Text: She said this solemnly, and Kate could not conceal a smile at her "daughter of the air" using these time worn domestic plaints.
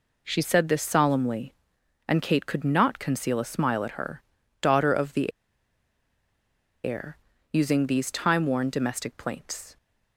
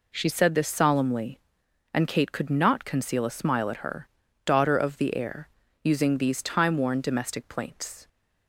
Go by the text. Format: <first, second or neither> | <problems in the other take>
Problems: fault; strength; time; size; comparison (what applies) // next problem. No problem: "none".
second | pauses between "her" and "daughter"; slight; at 4.2 s; 0.36 s long; slight in the second // pauses between "the" and "air"; strong; at 5.3 s; 1.5 s long // pauses between "air" and "using"; slight; at 7.1 s; 0.34 s long; slight in the second